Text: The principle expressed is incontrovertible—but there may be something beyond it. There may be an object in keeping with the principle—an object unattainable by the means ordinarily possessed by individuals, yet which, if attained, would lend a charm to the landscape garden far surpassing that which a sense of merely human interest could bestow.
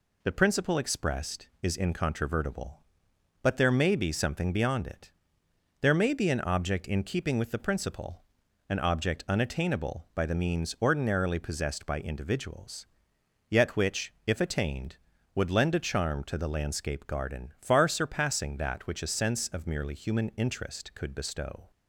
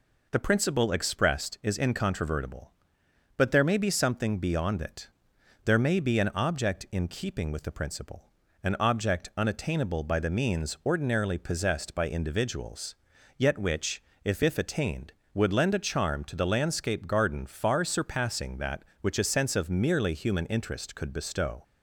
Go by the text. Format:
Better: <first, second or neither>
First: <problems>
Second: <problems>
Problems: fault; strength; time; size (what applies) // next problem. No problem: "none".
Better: first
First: none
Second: says "if" twice; at 14.4 s